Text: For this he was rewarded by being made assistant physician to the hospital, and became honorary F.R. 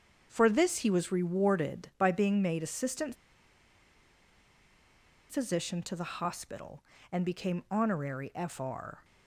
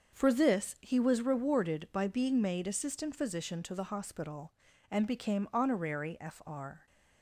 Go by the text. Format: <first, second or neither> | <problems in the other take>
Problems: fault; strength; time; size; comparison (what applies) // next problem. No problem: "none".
second | starts louder than the rest; until 1.3 s; 7 dB; also in the second // pauses between "assistant" and "physician"; strong; at 3.1 s; 2.1 s long